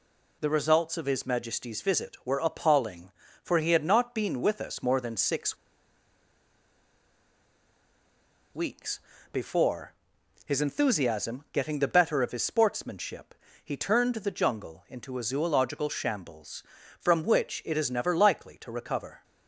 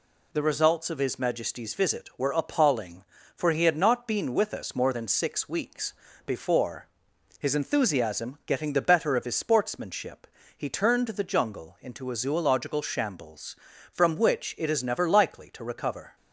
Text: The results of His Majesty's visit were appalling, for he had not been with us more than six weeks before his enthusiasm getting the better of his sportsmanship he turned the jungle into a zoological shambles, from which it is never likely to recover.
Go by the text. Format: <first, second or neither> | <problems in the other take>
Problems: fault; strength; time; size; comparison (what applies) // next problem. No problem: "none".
second | pauses between "six" and "weeks"; strong; at 5.5 s; 2.9 s long // pauses between "weeks" and "before"; slight; at 8.9 s; 0.32 s long; slight in the second // pauses between "before" and "his"; noticeable; at 9.9 s; 0.52 s long; noticeable in the second // pauses between "sportsmanship" and "he"; slight; at 13.3 s; 0.30 s long; slight in the second